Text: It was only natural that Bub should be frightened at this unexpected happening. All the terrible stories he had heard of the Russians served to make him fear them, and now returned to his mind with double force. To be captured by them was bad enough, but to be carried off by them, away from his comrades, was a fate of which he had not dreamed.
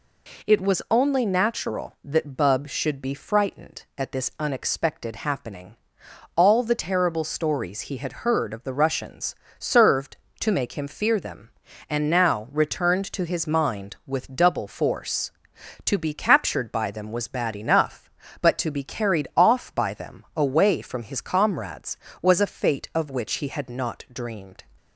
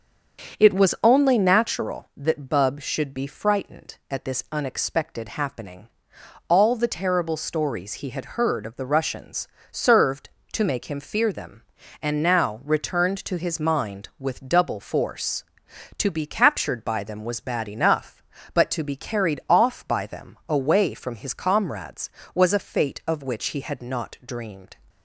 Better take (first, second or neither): first